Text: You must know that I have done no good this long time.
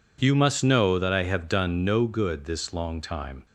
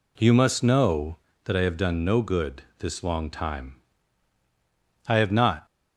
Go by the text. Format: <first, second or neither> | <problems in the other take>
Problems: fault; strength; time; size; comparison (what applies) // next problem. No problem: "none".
first | pauses between "good" and "this"; slight; at 2.6 s; 0.18 s long // goes on to say "I have not"; from 5.0 s on; 0.58 s long